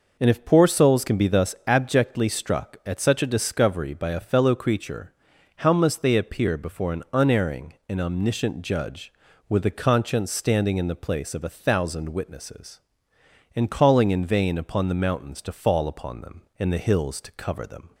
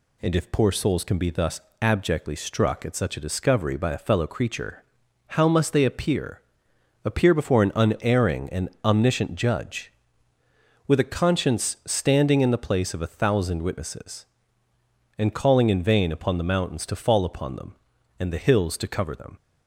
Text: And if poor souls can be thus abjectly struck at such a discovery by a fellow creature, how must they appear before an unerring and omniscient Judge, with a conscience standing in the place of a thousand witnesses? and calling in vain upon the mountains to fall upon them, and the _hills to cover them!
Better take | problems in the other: first | pauses between "thus" and "abjectly"; slight; at 1.6 s; 0.20 s long // says "appear" twice; at 7.0 s // pauses between "and" and "omniscient"; slight; at 8.6 s; 0.16 s long

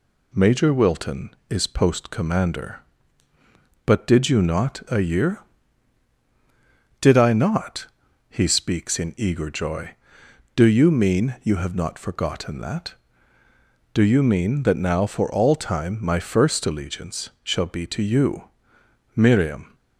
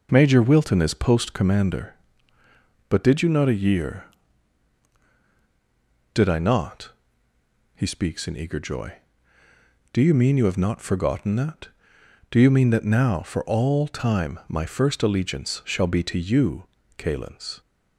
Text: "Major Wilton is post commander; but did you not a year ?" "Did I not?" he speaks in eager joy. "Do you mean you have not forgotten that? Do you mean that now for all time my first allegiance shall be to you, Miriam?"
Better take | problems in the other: first | says "Calens" for "Miriam"; at 16.9 s

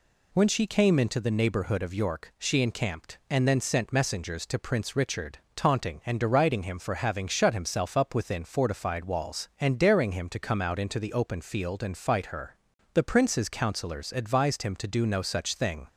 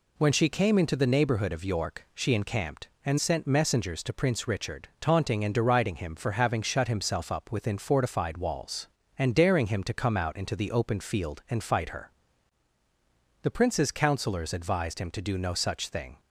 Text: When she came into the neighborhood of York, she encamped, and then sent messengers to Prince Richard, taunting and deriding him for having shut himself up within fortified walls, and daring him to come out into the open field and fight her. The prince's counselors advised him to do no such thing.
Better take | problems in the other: first | skips "then"; at 3.1 s

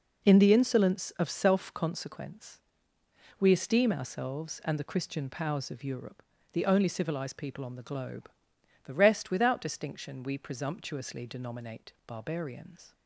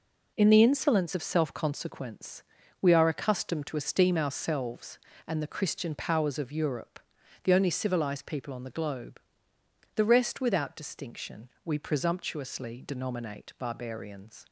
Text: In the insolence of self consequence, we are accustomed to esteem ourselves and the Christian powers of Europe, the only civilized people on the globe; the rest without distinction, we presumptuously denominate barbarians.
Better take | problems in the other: second | skips "are accustomed to"; at 3.5 s

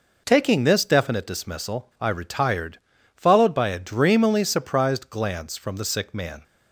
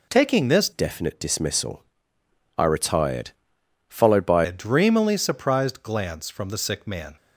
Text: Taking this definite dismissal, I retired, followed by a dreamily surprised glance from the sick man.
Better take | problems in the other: first | changes voice from "definite" to "by"; from 0.7 to 4.4 s; 3.7 s long

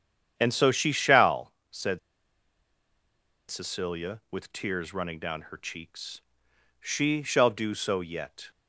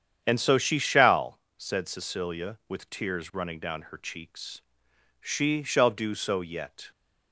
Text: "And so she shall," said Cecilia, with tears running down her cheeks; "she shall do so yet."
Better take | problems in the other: second | starts louder than the rest; strong; until 1.3 s; 8.5 dB; strong in the second // pauses between "said" and "Cecilia"; strong; at 1.9 s; 1.5 s long

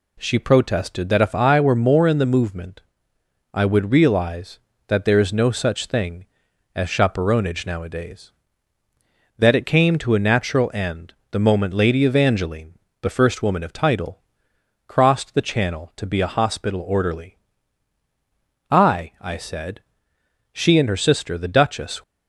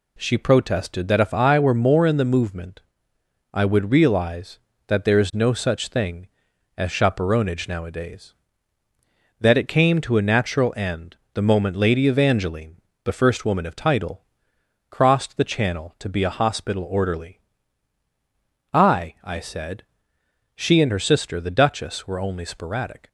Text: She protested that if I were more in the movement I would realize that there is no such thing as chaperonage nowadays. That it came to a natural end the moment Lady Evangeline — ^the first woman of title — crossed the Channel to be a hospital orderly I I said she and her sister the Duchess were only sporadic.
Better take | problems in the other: second | pauses between "movement" and "I"; noticeable; at 2.8 s; 0.72 s long; noticeable in the second // pauses between "end" and "the"; slight; at 11.1 s; 0.18 s long; slight in the second // pauses between "orderly" and "I"; strong; at 17.3 s; 1.3 s long; strong in the second // pauses between "said" and "she"; noticeable; at 19.8 s; 0.70 s long; noticeable in the second // stops before "were only sporadic"; at 22.0 s

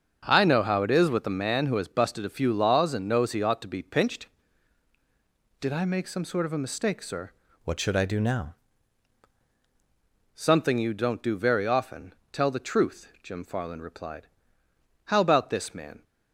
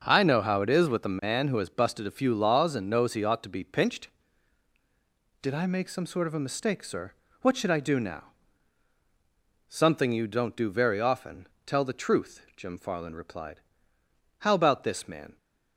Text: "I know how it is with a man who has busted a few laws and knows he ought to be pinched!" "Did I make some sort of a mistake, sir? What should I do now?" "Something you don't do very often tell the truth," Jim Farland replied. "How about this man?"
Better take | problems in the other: second | starts louder than the rest; until 1.2 s; 7 dB; also in the second // changes voice from "What" to "now"; from 7.6 to 8.5 s; 0.9 s long // pauses between "often" and "tell"; slight; at 12.1 s; 0.18 s long; slight in the second

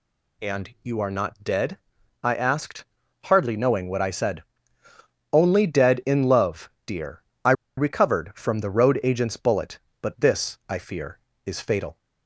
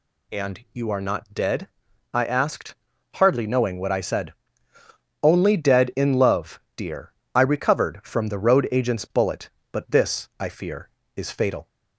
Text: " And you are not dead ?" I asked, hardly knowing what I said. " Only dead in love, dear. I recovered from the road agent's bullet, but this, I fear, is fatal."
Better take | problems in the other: second | pauses between "I" and "recovered"; slight; at 7.5 s; 0.24 s long

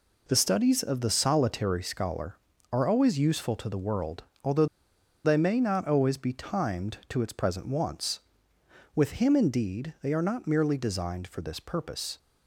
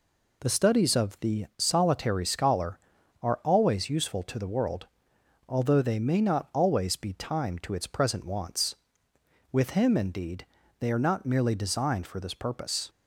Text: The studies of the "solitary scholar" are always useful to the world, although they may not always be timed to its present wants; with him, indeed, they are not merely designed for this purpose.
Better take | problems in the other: second | pauses between "although" and "they"; noticeable; at 4.6 s; 0.59 s long

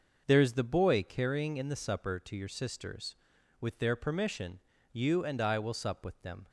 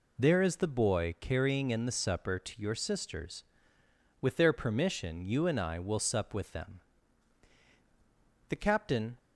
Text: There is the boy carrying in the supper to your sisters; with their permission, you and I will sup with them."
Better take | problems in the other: first | goes on to say "The captain"; noticeable; from 8.4 s on; 0.68 s long

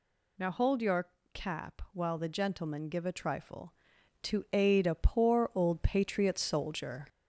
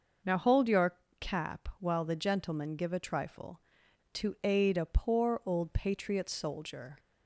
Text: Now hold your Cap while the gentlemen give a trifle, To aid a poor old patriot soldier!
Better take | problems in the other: second | gets louder; slight; throughout; 2 dB // pauses between "your" and "Cap"; slight; at 1.0 s; 0.26 s long; slight in the second

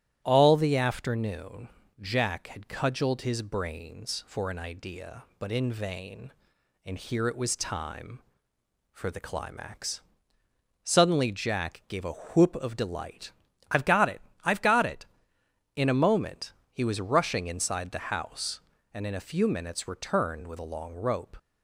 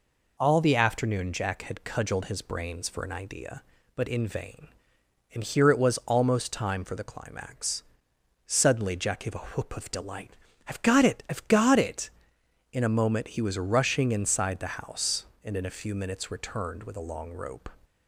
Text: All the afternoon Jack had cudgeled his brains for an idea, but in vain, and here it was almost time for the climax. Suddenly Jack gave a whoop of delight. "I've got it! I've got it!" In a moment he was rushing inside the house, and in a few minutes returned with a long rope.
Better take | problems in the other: second | starts louder than the rest; strong; until 1.2 s; 12 dB // pauses between "afternoon" and "Jack"; slight; at 1.6 s; 0.28 s long // skips "almost"; at 7.5 s // pauses between "moment" and "he"; slight; at 16.5 s; 0.18 s long

